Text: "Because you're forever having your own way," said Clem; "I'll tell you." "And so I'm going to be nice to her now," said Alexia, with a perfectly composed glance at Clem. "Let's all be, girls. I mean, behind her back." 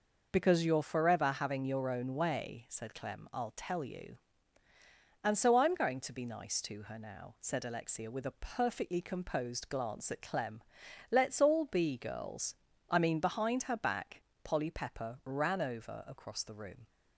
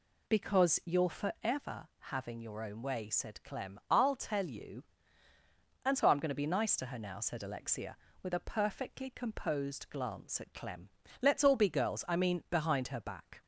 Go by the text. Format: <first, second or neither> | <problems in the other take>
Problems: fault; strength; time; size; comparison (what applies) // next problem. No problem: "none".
second | goes on to say "Polly Pepper ran over across the room"; strong; from 14.4 s on; 2.4 s long